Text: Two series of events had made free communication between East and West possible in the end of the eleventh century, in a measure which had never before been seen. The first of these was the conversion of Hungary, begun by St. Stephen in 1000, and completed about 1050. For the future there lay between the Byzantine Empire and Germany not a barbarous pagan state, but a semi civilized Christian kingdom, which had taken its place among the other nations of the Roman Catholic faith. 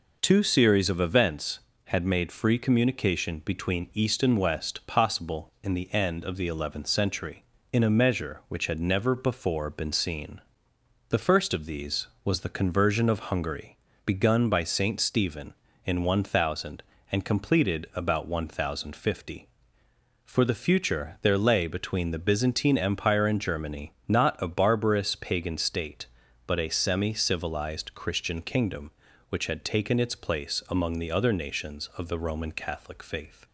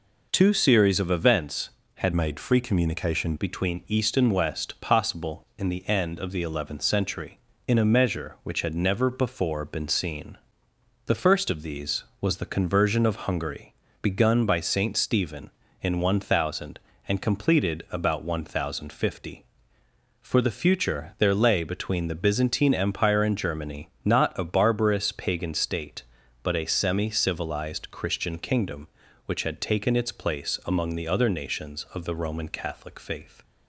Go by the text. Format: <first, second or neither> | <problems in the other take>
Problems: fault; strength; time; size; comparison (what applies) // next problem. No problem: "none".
first | changes voice from "made" to "communication"; from 2.1 to 3.3 s; 1.2 s long // pauses between "Germany" and "not"; slight; at 23.8 s; 0.16 s long; slight in the first